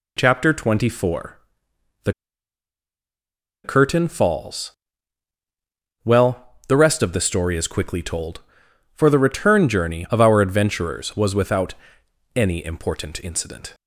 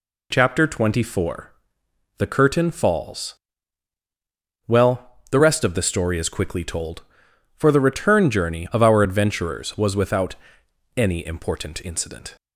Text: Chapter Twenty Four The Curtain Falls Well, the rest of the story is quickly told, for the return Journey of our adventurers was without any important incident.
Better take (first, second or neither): second